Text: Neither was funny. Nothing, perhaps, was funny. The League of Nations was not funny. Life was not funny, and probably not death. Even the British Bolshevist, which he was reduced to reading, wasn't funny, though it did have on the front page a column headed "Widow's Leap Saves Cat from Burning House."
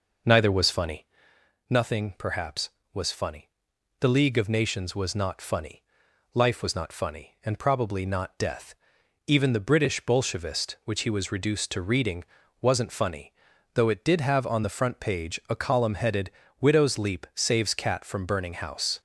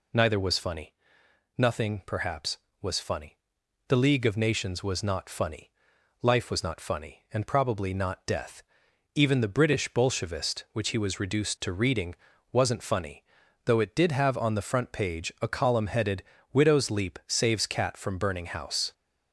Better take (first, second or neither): second